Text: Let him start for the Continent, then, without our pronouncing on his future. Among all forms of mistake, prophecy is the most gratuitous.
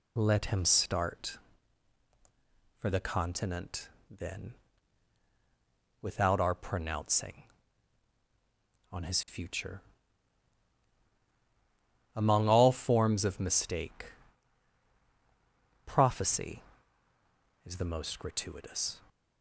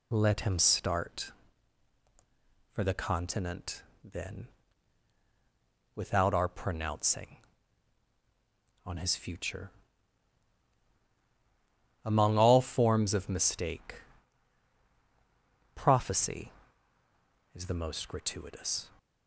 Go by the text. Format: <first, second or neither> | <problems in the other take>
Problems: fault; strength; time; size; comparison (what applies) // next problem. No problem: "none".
neither | none